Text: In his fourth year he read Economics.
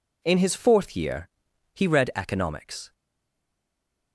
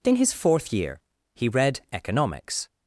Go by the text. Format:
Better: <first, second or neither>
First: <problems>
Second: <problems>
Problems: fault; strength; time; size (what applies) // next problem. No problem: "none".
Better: second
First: pauses between "year" and "he"; noticeable; at 1.2 s; 0.46 s long // stays silent after the last word; noticeable; from 2.9 s on; 1.2 s long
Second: pauses between "year" and "he"; at 0.9 s; 0.38 s long